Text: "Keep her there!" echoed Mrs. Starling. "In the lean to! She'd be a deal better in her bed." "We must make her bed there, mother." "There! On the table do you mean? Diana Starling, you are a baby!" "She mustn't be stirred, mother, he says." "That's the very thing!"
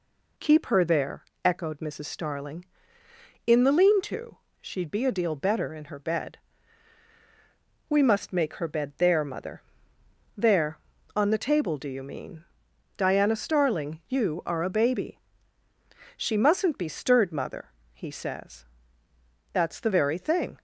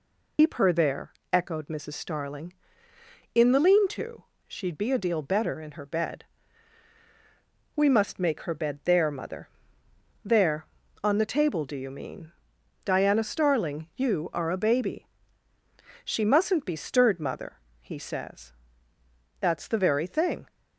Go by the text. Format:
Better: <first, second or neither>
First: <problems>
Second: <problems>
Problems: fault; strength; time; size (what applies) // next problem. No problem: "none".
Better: first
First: none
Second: loses the start of "Keep"; at 0.3 s; 120 ms